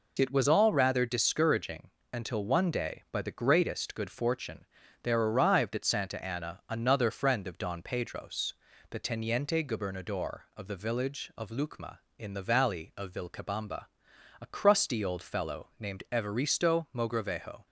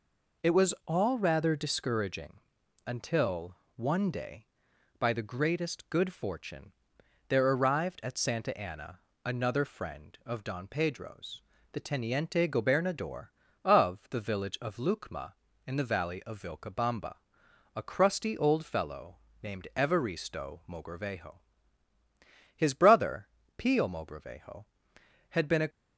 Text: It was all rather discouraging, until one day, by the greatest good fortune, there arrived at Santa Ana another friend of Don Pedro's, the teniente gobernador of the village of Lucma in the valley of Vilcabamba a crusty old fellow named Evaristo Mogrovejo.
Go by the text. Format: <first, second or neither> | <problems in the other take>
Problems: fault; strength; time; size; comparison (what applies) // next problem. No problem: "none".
first | pauses between "until" and "one"; slight; at 3.5 s; 0.20 s long // pauses between "Ana" and "another"; slight; at 8.9 s; 0.26 s long // pauses between "Vilcabamba" and "a"; noticeable; at 17.1 s; 0.60 s long; noticeable in the first // pauses between "fellow" and "named"; slight; at 19.1 s; 0.26 s long // goes on to say "His brother Pio Mogrovejo had been a"; strong; from 22.5 s on; 3.1 s long